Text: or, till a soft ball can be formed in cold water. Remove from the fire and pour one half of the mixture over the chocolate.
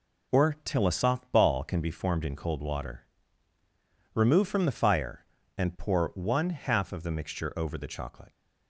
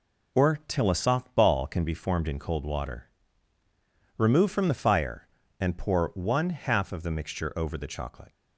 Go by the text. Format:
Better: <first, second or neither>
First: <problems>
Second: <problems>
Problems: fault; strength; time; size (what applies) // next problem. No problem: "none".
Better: neither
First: none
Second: none